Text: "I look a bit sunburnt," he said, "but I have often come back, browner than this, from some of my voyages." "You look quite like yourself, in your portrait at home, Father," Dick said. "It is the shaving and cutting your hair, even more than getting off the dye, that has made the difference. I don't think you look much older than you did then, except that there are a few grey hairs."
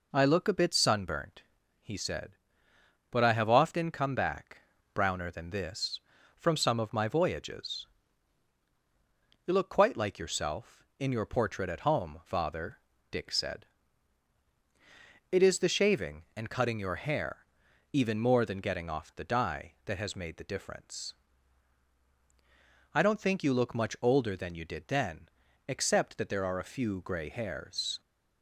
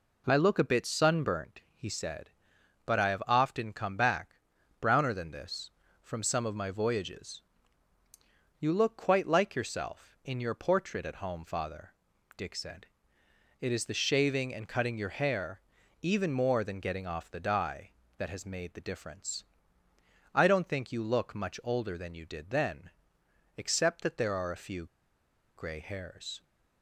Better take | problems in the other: first | pauses between "few" and "grey"; noticeable; at 24.8 s; 0.69 s long

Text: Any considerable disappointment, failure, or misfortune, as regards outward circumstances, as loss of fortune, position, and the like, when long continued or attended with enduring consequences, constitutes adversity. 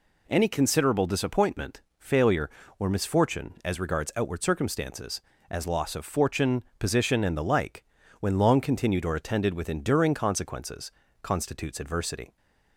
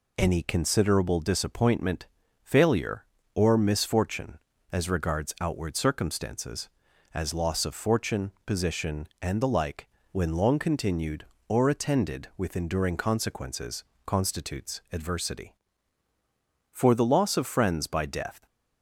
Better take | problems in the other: first | goes on to say "For the loss of friends by death"; strong; from 16.7 s on; 1.7 s long

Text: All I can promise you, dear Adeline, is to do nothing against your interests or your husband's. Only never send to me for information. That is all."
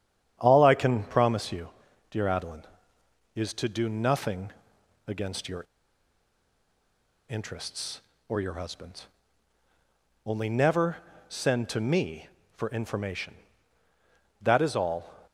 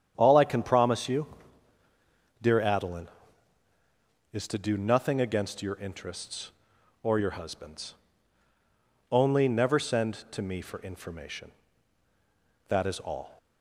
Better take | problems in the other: second | starts louder than the rest; strong; until 1.4 s; 9 dB; strong in the second // pauses between "nothing" and "against"; noticeable; at 4.5 s; 0.56 s long // pauses between "your" and "interests"; strong; at 5.6 s; 1.6 s long // pauses between "never" and "send"; slight; at 10.9 s; 0.32 s long

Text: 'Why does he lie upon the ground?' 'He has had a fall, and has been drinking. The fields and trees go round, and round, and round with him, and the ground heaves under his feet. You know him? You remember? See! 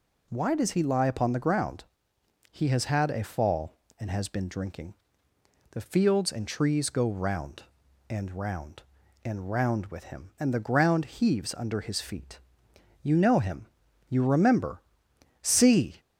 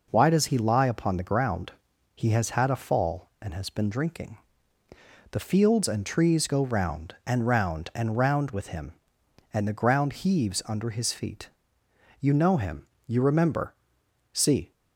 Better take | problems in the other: neither | none

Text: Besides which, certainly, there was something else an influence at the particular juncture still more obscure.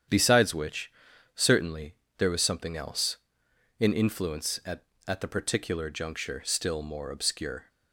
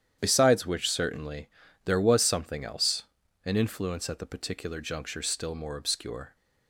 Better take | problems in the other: second | starts louder than the rest; strong; until 1.5 s; 9 dB; strong in the second // pauses between "else" and "an"; noticeable; at 3.1 s; 0.64 s long; also in the second // says "at" twice; at 5.0 s

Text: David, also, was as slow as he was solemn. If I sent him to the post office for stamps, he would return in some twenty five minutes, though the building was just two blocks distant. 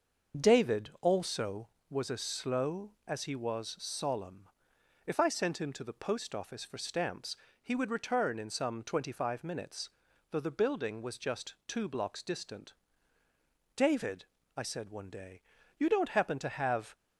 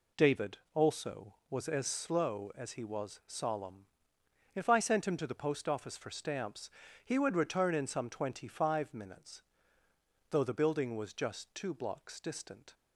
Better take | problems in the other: second | starts louder than the rest; until 1.5 s; 6 dB // goes on to say "David I said one day you don't happen to have"; strong; from 13.7 s on; 3.2 s long

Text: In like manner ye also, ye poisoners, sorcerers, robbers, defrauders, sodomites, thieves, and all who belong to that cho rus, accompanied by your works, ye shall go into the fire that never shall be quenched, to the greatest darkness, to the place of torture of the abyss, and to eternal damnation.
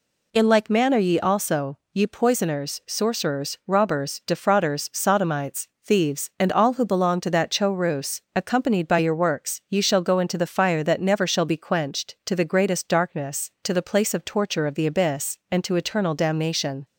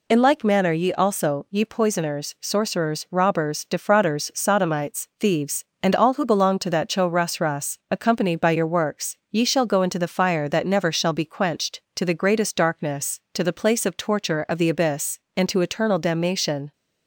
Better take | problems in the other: first | says "rus" twice; at 7.4 s

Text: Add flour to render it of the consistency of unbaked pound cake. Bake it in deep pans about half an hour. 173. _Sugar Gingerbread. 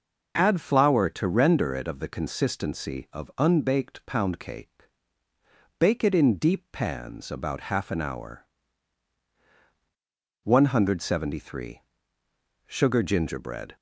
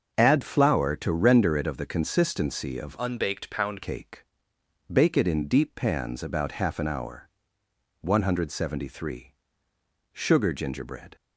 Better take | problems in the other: first | starts louder than the rest; until 1.1 s; 6.5 dB // changes voice from "unbaked" to "pound"; from 2.9 to 3.8 s; 0.9 s long

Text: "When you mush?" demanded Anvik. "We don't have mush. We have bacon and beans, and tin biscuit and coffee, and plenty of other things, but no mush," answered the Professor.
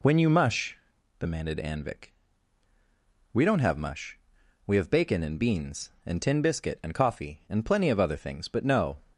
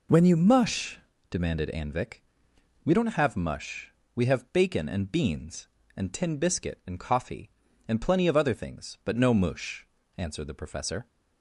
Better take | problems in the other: second | stops before "mush answered the Professor"; at 9.1 s

